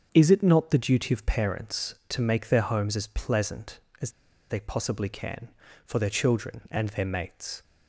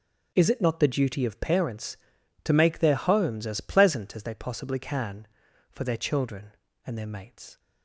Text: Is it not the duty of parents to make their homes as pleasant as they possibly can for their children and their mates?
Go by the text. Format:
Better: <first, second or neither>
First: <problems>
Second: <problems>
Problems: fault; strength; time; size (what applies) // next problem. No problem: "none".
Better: second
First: starts louder than the rest; until 1.1 s; 7 dB // pauses between "as" and "they"; at 4.0 s; 0.41 s long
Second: none